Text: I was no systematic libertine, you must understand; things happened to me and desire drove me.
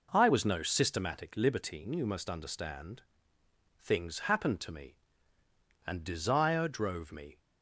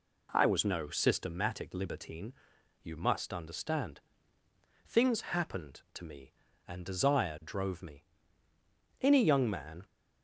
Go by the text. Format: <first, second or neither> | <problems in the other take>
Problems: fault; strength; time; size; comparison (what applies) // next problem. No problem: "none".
first | goes on to say "Any young man"; noticeable; from 8.9 s on; 0.86 s long